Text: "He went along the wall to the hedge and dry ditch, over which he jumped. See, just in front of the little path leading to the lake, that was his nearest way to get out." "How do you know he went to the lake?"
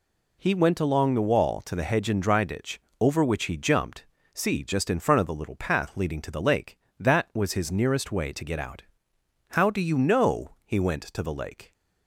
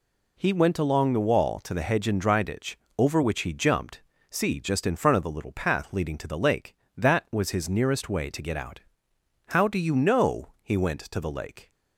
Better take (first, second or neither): neither